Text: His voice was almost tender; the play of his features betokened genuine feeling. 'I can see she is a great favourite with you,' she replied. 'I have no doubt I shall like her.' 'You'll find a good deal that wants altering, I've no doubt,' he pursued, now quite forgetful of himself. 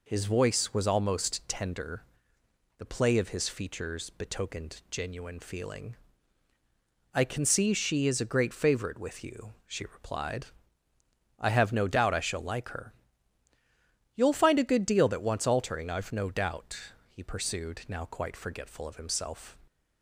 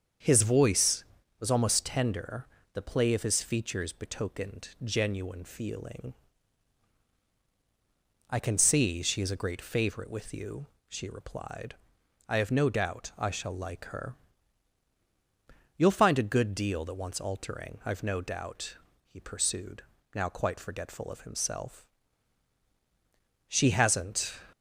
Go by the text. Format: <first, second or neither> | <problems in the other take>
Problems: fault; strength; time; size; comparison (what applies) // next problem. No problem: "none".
first | starts louder than the rest; strong; until 1.6 s; 7 dB // goes on to say "She hasn't"; noticeable; from 23.4 s on; 0.92 s long